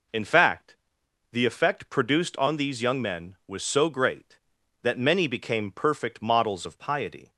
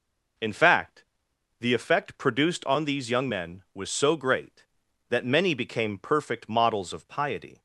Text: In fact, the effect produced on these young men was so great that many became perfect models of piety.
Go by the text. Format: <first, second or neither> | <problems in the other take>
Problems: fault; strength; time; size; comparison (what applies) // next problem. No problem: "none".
neither | none